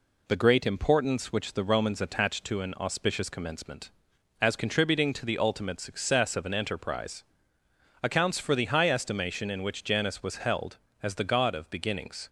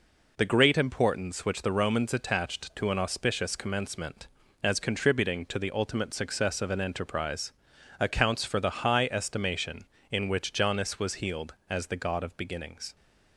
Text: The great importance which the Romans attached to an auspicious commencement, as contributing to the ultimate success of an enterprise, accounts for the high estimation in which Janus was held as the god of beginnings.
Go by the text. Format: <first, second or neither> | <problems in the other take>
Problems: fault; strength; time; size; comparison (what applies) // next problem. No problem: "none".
first | says "healed" for "held"; at 11.1 s